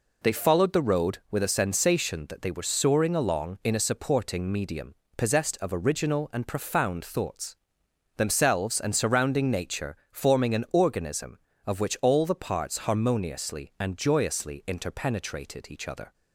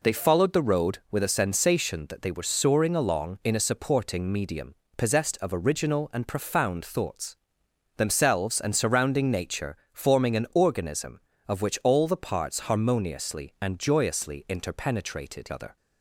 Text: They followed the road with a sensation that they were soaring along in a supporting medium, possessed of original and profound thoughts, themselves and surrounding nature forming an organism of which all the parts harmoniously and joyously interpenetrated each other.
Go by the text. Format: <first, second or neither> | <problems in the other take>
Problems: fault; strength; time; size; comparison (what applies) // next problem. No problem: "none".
first | pauses between "nature" and "forming"; slight; at 9.7 s; 0.16 s long // skips "each"; at 15.5 s